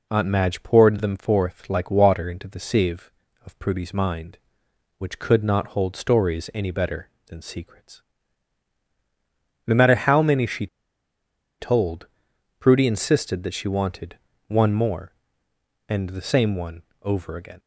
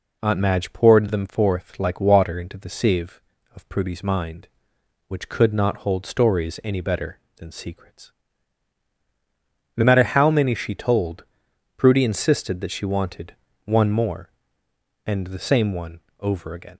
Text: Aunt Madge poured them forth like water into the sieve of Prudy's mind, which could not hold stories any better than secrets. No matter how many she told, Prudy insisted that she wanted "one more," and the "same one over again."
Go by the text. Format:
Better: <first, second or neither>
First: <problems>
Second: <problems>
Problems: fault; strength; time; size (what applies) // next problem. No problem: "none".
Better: second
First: pauses between "she" and "told"; noticeable; at 10.6 s; 0.93 s long // pauses between "wanted" and "one"; slight; at 14.1 s; 0.30 s long // pauses between "one" and "over"; slight; at 16.8 s; 0.20 s long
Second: pauses between "wanted" and "one"; slight; at 13.3 s; 0.30 s long // pauses between "one" and "over"; slight; at 16.0 s; 0.20 s long